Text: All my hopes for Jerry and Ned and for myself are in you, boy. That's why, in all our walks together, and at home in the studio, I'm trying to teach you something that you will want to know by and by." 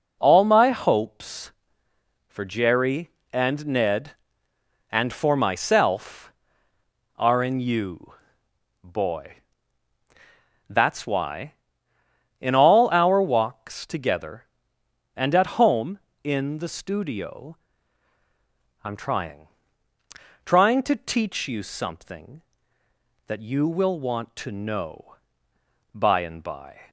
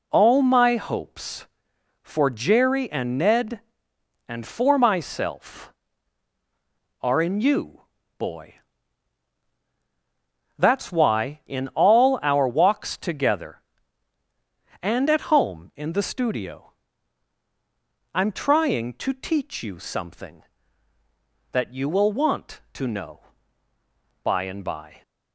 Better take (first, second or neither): second